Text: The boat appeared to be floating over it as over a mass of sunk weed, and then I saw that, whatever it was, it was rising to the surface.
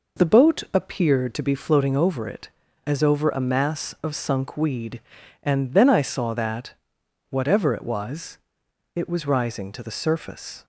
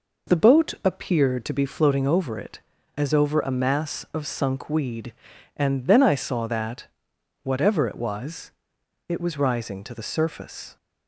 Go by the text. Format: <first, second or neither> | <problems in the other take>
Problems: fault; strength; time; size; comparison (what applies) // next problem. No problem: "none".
neither | none